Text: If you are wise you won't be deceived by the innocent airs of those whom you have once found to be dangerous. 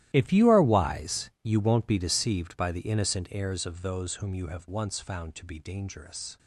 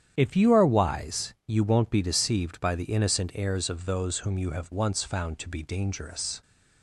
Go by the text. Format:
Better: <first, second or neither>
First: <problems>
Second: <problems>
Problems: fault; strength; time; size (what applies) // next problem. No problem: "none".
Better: second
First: gets quieter; strong; throughout; 17.5 dB // starts louder than the rest; strong; until 1.1 s; 14 dB // pauses between "wise" and "you"; slight; at 1.2 s; 0.16 s long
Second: starts louder than the rest; strong; until 1.1 s; 9.5 dB // pauses between "wise" and "you"; slight; at 1.3 s; 0.16 s long